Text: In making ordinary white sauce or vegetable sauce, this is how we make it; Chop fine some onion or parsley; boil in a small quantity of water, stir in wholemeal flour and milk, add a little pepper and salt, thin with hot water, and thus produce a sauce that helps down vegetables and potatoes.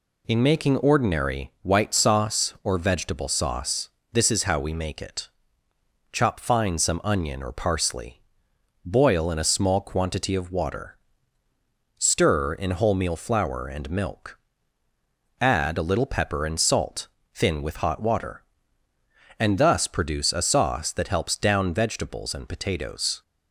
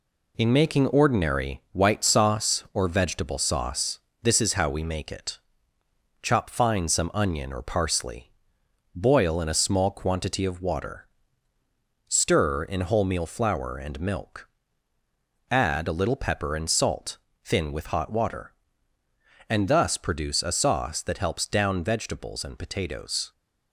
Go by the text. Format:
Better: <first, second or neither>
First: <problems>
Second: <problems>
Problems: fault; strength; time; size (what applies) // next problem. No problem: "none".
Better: first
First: none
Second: gets quieter; noticeable; throughout; 5 dB